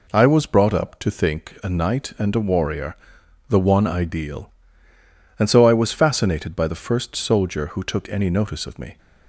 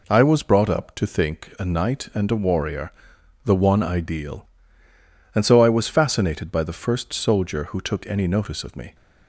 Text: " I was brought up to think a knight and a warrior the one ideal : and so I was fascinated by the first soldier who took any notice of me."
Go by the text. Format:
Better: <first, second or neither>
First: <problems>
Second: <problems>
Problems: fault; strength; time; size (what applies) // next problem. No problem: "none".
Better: neither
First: pauses between "warrior" and "the"; noticeable; at 2.9 s; 0.54 s long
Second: pauses between "warrior" and "the"; noticeable; at 2.9 s; 0.54 s long